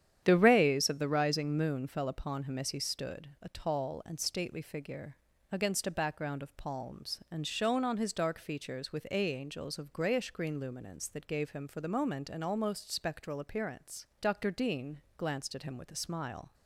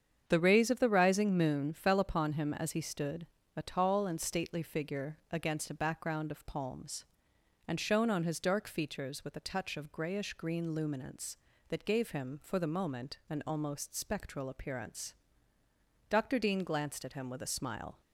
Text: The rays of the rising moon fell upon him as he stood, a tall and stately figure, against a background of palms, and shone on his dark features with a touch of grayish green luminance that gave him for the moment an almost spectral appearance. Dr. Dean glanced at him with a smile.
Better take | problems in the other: second | starts louder than the rest; strong; until 1.2 s; 9.5 dB; strong in the second // says "angels" for "touch"; at 9.3 s // pauses between "Dean" and "glanced"; slight; at 15.0 s; 0.16 s long

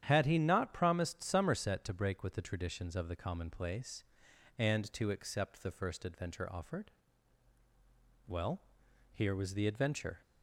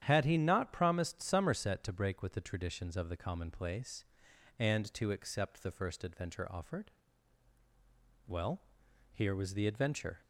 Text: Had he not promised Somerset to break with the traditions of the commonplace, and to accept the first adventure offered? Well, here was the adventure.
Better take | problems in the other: neither | starts louder than the rest; strong; the same in both

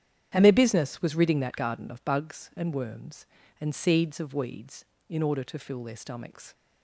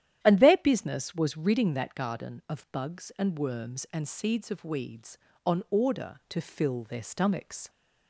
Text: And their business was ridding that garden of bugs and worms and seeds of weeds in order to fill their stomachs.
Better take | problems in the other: first | starts louder than the rest; strong; until 1.2 s; 11 dB; strong in the first // says "on" for "in"; at 5.4 s

